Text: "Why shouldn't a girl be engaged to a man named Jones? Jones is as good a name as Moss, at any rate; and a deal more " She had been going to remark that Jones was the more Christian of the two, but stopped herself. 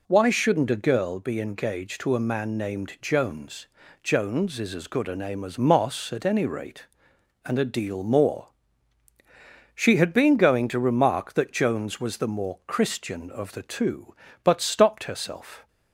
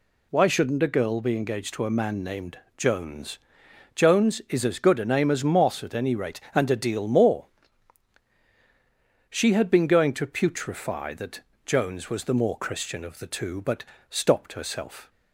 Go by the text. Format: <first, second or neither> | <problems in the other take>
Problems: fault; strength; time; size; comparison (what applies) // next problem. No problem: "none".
first | pauses between "named" and "Jones"; slight; at 2.5 s; 0.18 s long // says "putrefy" for "remark"; at 10.2 s // pauses between "that" and "Jones"; slight; at 11.3 s; 0.24 s long // pauses between "but" and "stopped"; slight; at 13.8 s; 0.24 s long